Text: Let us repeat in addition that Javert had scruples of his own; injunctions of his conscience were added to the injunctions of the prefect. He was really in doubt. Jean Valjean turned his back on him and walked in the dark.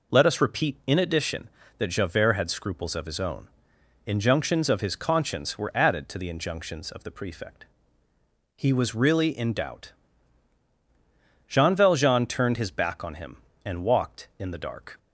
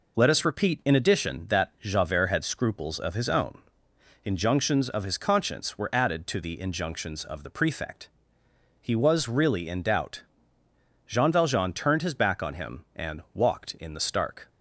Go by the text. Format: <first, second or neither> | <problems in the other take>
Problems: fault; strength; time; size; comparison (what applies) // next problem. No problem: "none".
first | says "stark" for "dark"; at 13.9 s